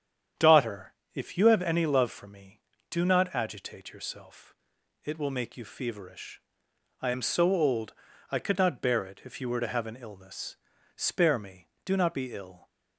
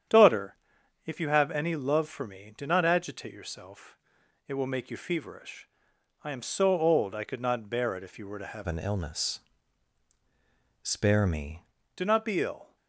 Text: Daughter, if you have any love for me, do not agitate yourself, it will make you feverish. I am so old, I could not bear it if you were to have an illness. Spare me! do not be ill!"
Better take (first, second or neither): first